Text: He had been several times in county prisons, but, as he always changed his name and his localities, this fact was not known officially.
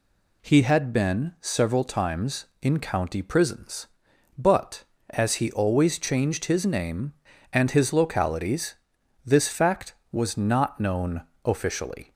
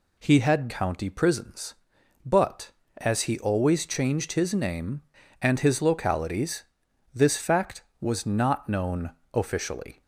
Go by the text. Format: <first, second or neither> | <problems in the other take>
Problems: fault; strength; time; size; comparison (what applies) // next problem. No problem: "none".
first | skips "been several times in"; at 0.6 s // pauses between "known" and "officially"; slight; at 9.1 s; 0.22 s long; slight in the first